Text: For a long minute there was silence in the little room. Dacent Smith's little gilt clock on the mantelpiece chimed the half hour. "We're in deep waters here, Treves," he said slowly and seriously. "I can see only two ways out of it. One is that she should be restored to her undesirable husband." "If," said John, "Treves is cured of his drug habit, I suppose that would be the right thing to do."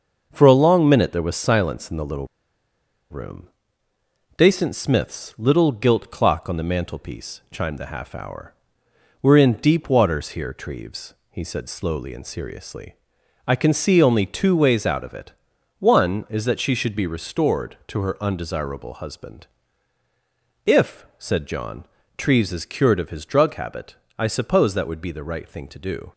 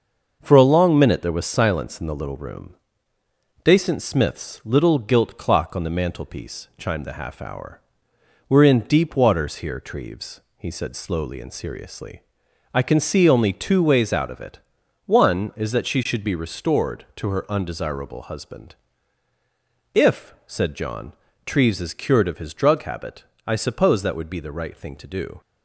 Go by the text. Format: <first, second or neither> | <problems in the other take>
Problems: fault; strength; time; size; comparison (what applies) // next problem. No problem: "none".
second | starts louder than the rest; until 1.3 s; 6.5 dB; also in the second // pauses between "little" and "room"; noticeable; at 2.2 s; 0.83 s long